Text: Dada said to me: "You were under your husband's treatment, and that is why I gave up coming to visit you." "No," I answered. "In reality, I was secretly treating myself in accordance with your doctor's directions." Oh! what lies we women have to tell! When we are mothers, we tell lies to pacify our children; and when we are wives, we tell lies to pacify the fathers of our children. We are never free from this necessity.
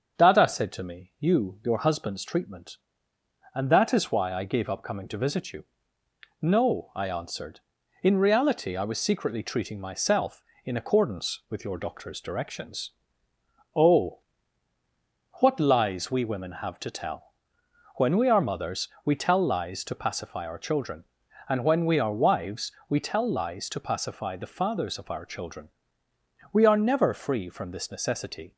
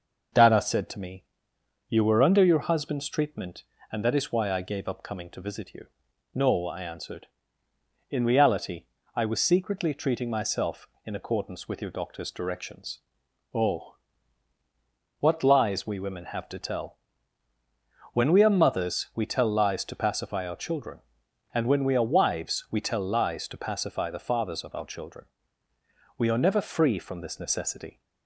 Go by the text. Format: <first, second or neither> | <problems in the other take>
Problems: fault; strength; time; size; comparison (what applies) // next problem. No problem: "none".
second | starts louder than the rest; until 1.2 s; 6.5 dB // skips "were under"; at 1.6 s